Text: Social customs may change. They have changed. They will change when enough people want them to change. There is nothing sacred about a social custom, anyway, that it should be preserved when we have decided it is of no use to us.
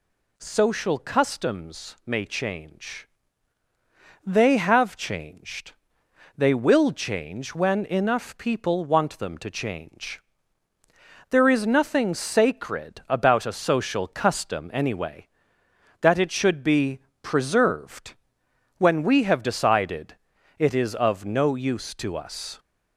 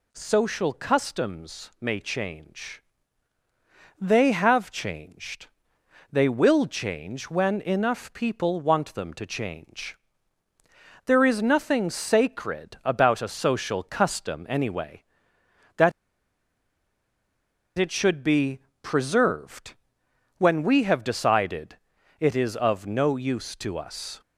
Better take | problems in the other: first | pauses between "that" and "it"; strong; at 15.9 s; 1.8 s long // pauses between "be" and "preserved"; slight; at 18.5 s; 0.24 s long; slight in the first // pauses between "preserved" and "when"; noticeable; at 19.7 s; 0.62 s long; noticeable in the first // pauses between "decided" and "it"; at 21.7 s; 0.42 s long; also in the first

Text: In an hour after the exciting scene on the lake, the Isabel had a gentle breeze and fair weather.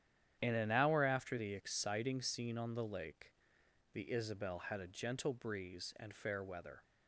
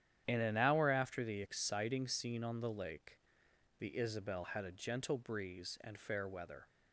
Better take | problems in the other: neither | starts louder than the rest; strong; the same in both

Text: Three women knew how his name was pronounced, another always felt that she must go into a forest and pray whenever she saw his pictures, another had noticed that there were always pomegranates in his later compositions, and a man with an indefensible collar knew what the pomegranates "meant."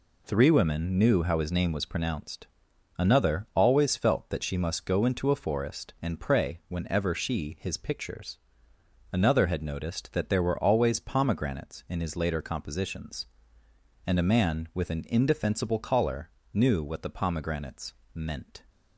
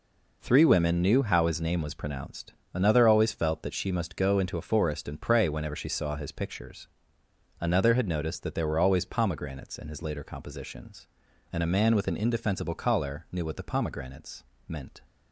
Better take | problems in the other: second | skips "saw"; at 7.5 s // pauses between "collar" and "knew"; slight; at 16.3 s; 0.24 s long // pauses between "pomegranates" and "meant"; slight; at 17.9 s; 0.22 s long; slight in the second

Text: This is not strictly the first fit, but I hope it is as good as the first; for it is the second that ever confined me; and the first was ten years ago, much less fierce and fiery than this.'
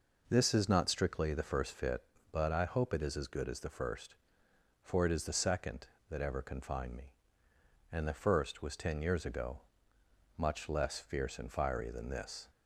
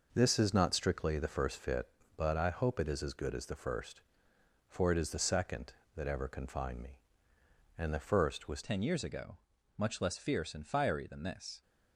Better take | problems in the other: first | changes voice at "ten"; from 8.6 s on; 3.0 s long

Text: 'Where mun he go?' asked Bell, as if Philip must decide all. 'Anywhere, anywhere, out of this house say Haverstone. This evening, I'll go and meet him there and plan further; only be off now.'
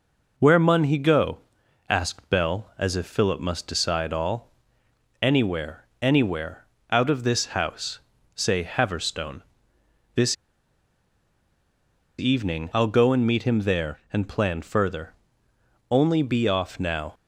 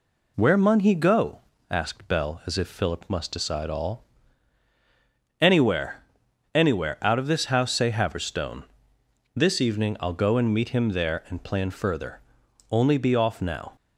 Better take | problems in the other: second | pauses between "house" and "say"; slight; at 8.0 s; 0.34 s long // pauses between "This" and "evening"; strong; at 10.3 s; 1.8 s long

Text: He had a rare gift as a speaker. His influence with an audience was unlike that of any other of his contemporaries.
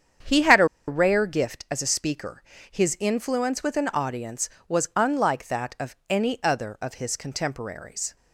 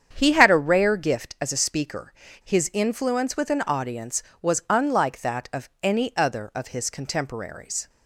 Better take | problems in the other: second | starts louder than the rest; strong; until 1.4 s; 8 dB; strong in the second // pauses between "a" and "rare"; slight; at 0.6 s; 0.22 s long

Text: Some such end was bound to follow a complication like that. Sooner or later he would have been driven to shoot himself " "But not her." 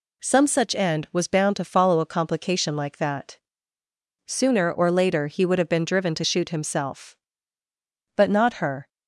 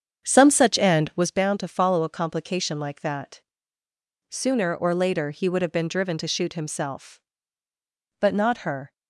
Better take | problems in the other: first | starts louder than the rest; strong; until 1.3 s; 8 dB

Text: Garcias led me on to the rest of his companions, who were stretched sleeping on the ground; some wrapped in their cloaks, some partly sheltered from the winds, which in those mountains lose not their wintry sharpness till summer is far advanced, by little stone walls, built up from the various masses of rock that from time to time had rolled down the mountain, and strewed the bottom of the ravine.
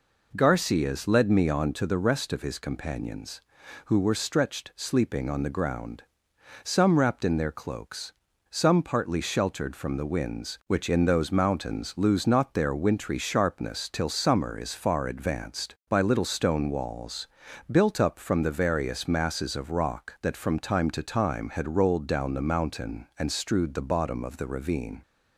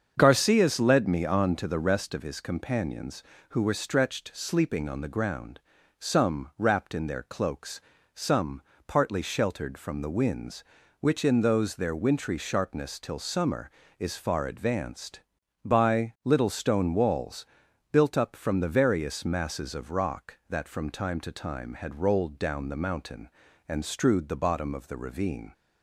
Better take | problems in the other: first | starts louder than the rest; until 1.1 s; 7 dB // pauses between "some" and "partly"; slight; at 8.6 s; 0.24 s long // skips "mountains lose not"; at 11.7 s

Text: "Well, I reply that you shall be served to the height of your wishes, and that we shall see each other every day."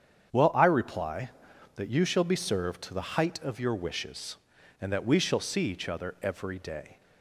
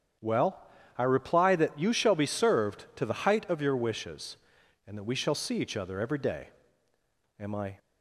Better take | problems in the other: first | starts louder than the rest; strong; until 1.5 s; 8.5 dB; strong in the first // goes on to say "Am I"; slight; from 7.3 s on; 0.40 s long

